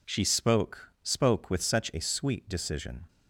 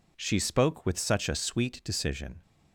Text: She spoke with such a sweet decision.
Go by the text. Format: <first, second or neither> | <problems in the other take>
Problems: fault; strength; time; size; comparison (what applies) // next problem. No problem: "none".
second | says "spoke" twice; at 1.0 s